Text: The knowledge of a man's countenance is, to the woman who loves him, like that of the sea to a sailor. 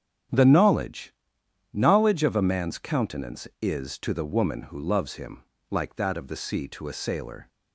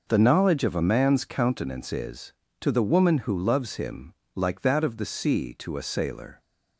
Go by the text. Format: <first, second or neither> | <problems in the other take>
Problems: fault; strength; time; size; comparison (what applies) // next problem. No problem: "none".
second | starts louder than the rest; strong; until 1.9 s; 9 dB // says "knowledge" twice; at 1.7 s